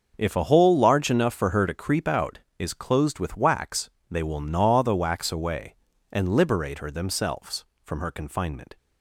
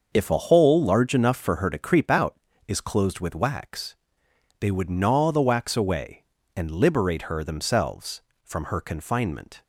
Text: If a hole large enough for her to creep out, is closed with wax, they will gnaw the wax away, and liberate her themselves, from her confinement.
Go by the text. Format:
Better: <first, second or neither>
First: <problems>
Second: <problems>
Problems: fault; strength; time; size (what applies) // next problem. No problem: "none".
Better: first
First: starts louder than the rest; until 1.1 s; 6.5 dB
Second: starts louder than the rest; until 1.1 s; 6.5 dB // says "would" for "will"; at 4.6 s